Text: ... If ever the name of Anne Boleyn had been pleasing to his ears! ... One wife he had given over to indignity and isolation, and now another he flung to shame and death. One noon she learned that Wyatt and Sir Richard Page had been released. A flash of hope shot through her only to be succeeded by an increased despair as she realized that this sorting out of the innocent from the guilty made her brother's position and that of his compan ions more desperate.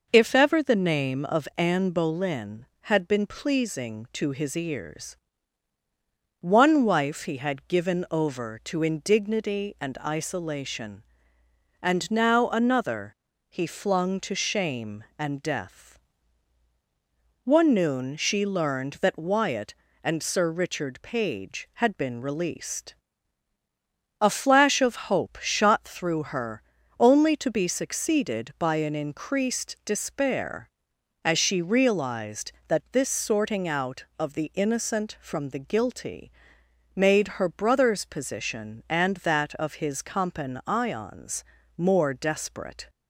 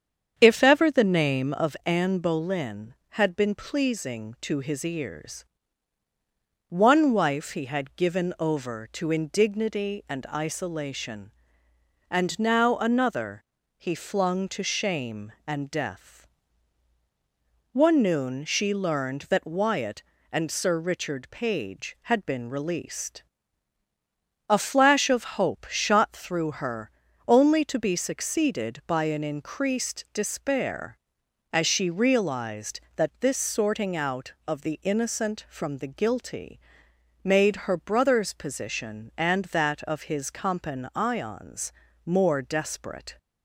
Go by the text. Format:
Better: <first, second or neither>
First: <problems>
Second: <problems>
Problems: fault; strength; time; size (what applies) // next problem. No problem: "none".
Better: first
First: pauses between "another" and "he"; slight; at 13.1 s; 0.34 s long // pauses between "her" and "only"; at 26.6 s; 0.38 s long // pauses between "guilty" and "made"; noticeable; at 36.2 s; 0.68 s long // pauses between "ions" and "more"; slight; at 41.4 s; 0.32 s long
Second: starts louder than the rest; strong; until 1.7 s; 8 dB // pauses between "another" and "he"; slight; at 13.4 s; 0.34 s long // pauses between "her" and "only"; at 26.9 s; 0.38 s long // pauses between "guilty" and "made"; noticeable; at 36.5 s; 0.68 s long // pauses between "ions" and "more"; slight; at 41.7 s; 0.32 s long